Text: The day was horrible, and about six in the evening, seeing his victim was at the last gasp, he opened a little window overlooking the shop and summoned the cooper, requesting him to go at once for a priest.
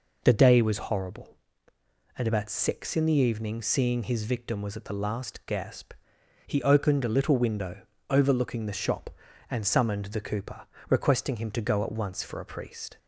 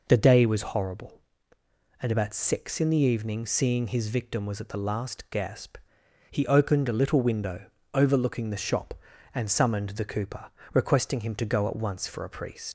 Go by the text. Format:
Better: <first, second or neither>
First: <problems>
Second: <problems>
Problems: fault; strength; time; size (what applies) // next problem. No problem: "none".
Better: first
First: pauses between "window" and "overlooking"; slight; at 7.8 s; 0.24 s long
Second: pauses between "window" and "overlooking"; slight; at 7.6 s; 0.24 s long // leaves "priest" unfinished; at 12.6 s; 80 ms